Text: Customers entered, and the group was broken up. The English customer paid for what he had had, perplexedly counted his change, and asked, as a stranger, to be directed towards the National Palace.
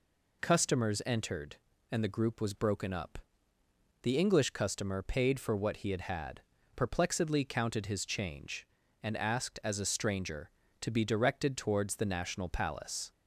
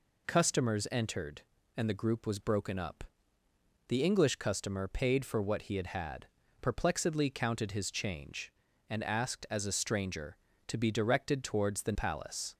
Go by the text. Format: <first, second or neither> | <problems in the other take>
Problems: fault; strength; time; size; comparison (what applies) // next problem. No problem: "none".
first | skips "National"; at 11.9 s